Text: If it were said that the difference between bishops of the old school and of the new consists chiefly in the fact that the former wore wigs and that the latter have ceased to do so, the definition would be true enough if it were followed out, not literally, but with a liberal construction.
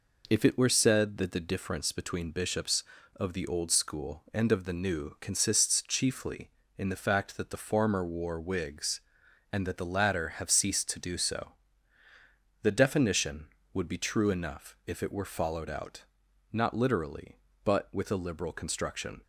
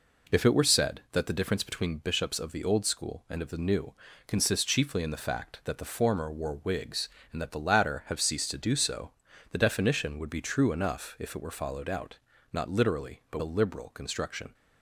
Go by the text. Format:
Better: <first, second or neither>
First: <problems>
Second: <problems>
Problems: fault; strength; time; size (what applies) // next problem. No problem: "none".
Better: first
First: none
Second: pauses between "new" and "consists"; slight; at 3.9 s; 0.34 s long // skips "with"; at 13.3 s